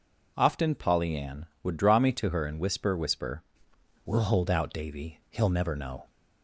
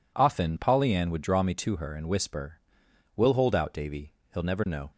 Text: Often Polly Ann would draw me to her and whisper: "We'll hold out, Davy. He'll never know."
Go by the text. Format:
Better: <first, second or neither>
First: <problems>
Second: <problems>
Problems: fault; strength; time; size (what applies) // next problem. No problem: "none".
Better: second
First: says "whisper" twice; at 2.9 s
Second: none